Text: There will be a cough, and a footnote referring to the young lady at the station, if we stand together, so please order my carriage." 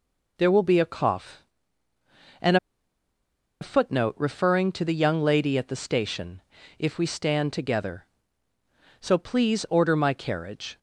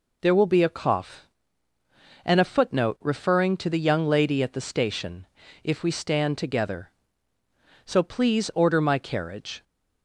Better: second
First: pauses between "and" and "a"; at 2.5 s; 1.0 s long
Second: none

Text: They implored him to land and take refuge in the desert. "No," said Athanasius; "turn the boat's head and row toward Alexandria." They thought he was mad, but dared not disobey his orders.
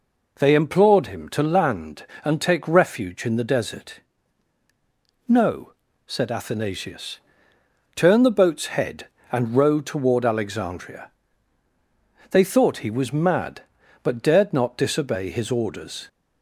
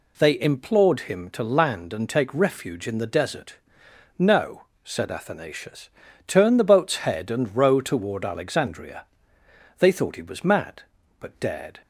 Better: first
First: none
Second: stops before "not disobey his orders"; at 11.8 s

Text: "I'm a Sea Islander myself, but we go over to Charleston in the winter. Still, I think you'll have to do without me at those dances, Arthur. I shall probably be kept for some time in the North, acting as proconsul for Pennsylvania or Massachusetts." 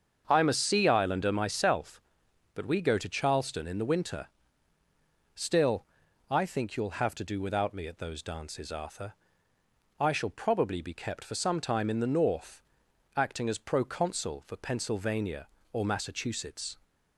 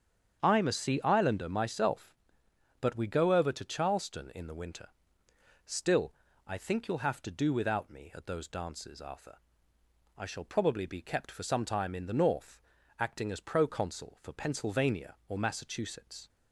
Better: second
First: starts louder than the rest; until 1.2 s; 7 dB // skips "over"; at 2.9 s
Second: starts louder than the rest; strong; until 1.4 s; 8 dB

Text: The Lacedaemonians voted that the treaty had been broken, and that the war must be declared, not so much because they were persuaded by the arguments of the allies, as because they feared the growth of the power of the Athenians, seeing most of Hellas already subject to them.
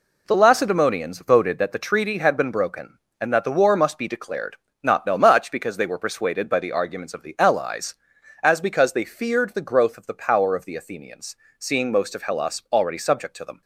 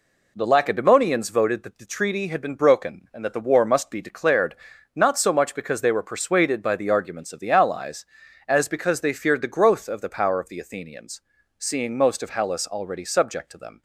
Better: second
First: says "no" for "so"; at 5.0 s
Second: none

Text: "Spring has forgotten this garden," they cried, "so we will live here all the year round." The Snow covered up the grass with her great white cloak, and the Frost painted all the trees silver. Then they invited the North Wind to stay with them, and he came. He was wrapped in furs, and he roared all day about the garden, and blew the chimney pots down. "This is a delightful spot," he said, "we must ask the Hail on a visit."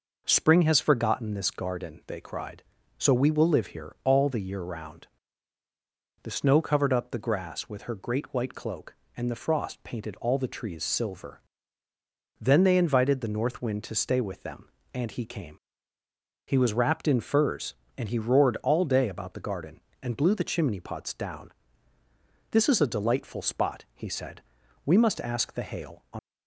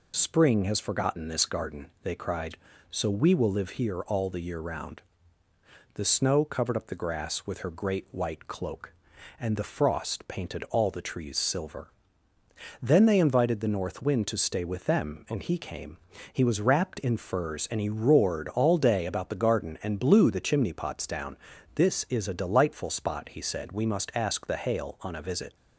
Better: second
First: stops before "a visit"; at 26.1 s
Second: none

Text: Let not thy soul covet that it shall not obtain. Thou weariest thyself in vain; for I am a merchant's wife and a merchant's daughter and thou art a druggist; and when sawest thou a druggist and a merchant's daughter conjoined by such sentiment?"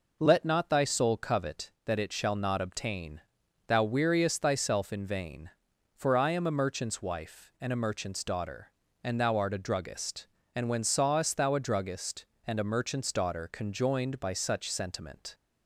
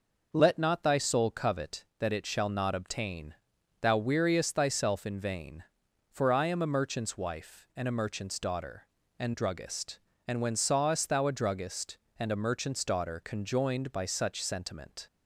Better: first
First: none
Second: skips "thou art a"; at 9.3 s

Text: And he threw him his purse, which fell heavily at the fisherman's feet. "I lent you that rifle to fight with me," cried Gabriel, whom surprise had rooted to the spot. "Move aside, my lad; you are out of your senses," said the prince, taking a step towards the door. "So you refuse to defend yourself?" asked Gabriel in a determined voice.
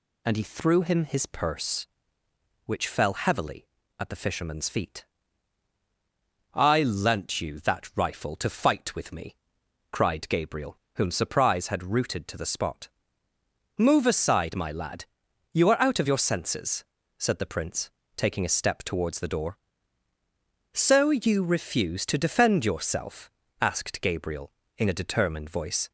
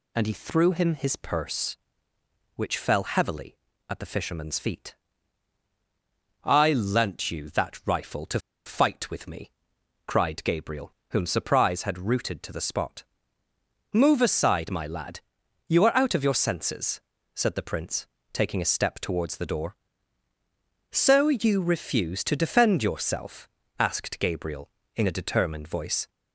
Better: first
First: none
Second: pauses between "to" and "fight"; slight; at 8.3 s; 0.26 s long

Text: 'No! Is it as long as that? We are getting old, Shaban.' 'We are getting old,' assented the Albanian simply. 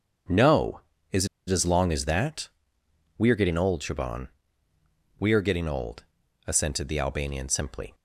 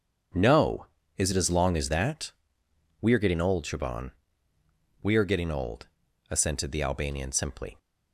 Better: second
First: starts louder than the rest; strong; until 1.8 s; 7.5 dB // pauses between "Is" and "it"; slight; at 1.2 s; 0.21 s long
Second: starts louder than the rest; strong; until 1.6 s; 7.5 dB

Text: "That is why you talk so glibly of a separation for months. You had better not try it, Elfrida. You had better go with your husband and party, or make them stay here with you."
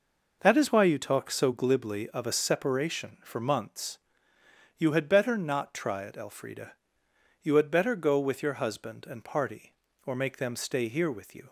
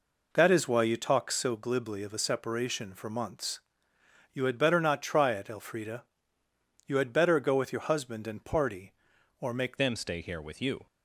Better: first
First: none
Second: changes voice at "them"; from 9.7 s on; 1.1 s long

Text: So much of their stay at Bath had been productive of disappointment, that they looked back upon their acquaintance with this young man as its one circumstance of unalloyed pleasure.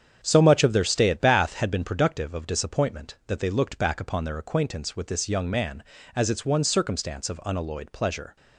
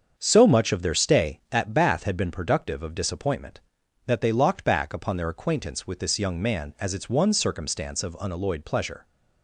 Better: first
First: starts louder than the rest; strong; until 1.2 s; 8 dB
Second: starts louder than the rest; until 1.1 s; 7 dB // says "locked" for "looked"; at 4.3 s

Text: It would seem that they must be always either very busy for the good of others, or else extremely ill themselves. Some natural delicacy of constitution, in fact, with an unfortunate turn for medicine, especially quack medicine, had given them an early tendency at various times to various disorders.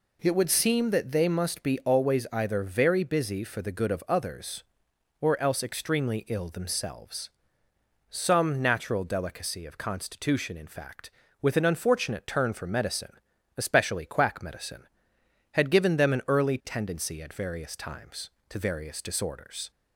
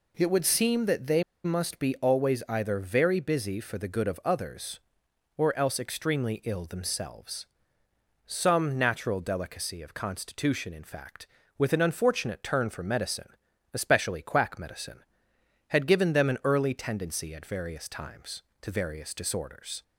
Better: first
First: none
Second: pauses between "they" and "must"; slight; at 1.2 s; 0.21 s long

